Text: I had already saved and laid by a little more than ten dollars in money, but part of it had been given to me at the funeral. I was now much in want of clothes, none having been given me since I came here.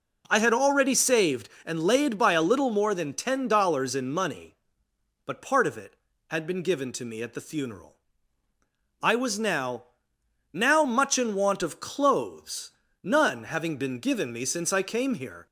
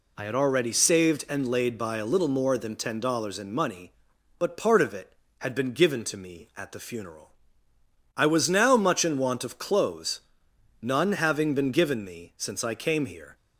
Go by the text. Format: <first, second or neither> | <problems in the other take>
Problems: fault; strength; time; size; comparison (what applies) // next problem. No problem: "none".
second | says "now" twice; at 10.5 s